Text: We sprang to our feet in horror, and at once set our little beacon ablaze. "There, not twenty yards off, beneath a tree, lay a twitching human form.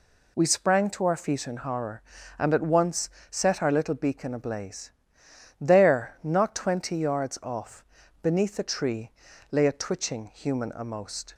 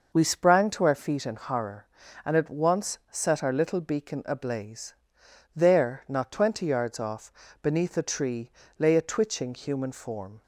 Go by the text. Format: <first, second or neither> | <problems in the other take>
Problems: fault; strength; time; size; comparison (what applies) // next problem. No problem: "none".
second | pauses between "once" and "set"; slight; at 3.0 s; 0.20 s long // says "amost" for "form"; at 10.6 s